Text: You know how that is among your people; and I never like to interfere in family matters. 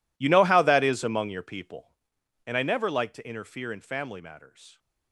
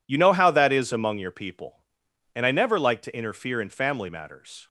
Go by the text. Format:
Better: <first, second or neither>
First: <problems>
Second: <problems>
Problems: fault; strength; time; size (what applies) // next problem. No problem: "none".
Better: second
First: gets quieter; strong; throughout; 21 dB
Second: none